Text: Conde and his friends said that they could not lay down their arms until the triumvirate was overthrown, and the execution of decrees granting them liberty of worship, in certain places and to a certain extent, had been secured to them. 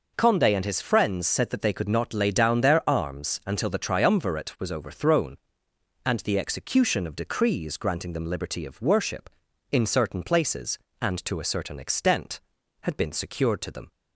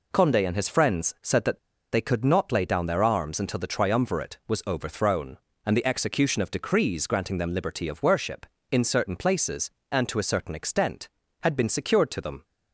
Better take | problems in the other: first | pauses between "that" and "they"; slight; at 1.5 s; 0.33 s long

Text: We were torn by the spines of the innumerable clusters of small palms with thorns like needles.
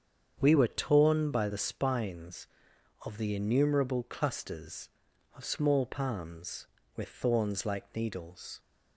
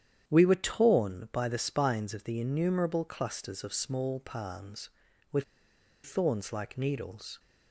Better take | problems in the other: first | starts louder than the rest; strong; until 1.2 s; 9.5 dB; strong in the first // pauses between "with" and "thorns"; noticeable; at 5.4 s; 0.60 s long

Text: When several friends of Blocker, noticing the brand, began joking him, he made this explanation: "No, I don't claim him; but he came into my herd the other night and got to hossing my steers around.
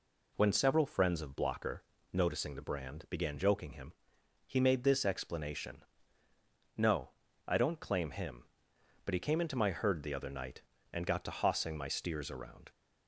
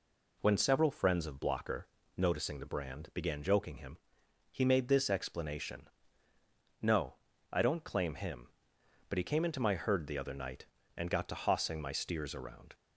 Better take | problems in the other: neither | none

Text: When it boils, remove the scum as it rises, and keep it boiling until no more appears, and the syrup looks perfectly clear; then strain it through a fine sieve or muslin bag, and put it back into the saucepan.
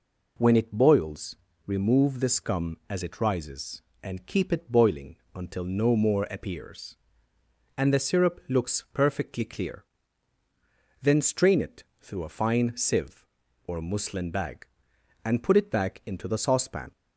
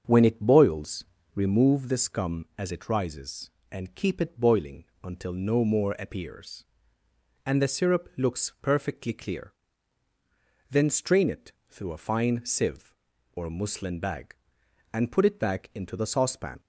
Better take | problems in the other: first | starts louder than the rest; until 1.8 s; 7 dB // pauses between "boiling" and "until"; slight; at 4.8 s; 0.18 s long; slight in the first // pauses between "it" and "through"; slight; at 11.5 s; 0.18 s long; slight in the first

